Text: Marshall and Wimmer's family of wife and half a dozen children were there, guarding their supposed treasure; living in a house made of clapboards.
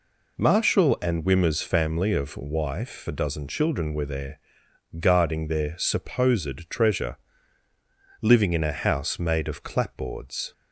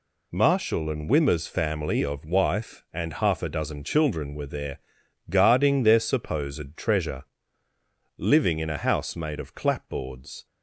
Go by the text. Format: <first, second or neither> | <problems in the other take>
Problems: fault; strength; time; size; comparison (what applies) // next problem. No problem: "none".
second | skips "and half"; at 3.0 s